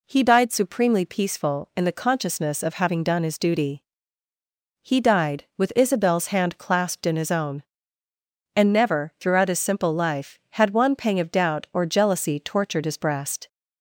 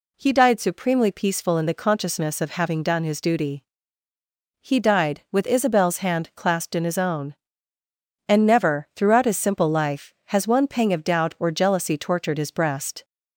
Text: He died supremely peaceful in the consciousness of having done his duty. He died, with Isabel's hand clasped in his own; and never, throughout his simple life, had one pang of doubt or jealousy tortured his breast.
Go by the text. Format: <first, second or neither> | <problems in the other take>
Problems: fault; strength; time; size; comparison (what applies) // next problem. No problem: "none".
first | says "has" for "had"; at 10.2 s